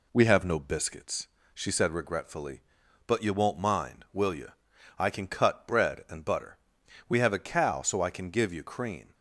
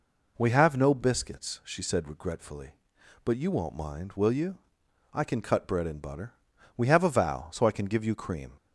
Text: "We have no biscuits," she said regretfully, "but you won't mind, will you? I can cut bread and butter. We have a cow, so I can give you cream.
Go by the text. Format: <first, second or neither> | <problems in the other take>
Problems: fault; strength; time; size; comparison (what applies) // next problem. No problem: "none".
first | says "vow" for "cow"; at 7.0 s